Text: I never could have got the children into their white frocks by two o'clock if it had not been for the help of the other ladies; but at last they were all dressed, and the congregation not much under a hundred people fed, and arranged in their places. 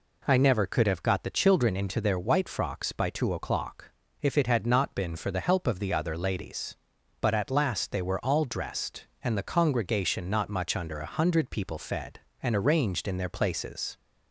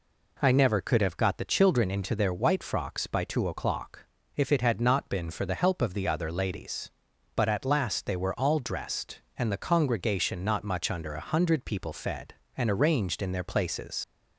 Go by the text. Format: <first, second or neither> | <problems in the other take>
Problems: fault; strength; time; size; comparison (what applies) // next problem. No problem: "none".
first | pauses between "o'clock" and "if"; slight; at 4.0 s; 0.30 s long; slight in the first // leaves "places" unfinished; at 14.0 s; 80 ms